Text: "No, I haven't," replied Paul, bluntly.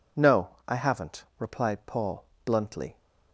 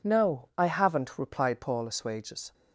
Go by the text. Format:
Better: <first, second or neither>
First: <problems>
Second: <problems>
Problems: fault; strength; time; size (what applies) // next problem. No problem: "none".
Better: first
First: none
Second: says "assuages" for "bluntly"; at 1.8 s